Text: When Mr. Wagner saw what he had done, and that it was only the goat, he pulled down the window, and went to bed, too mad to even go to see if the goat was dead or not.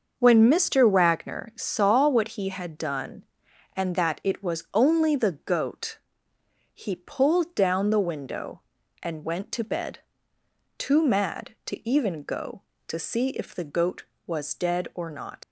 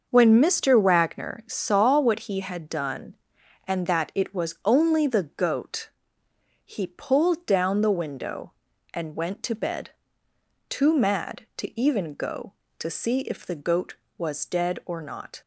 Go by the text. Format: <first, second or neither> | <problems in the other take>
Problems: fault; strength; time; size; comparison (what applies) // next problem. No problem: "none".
second | starts louder than the rest; until 1.1 s; 6.5 dB; also in the second // leaves "not" unfinished; at 15.4 s; 70 ms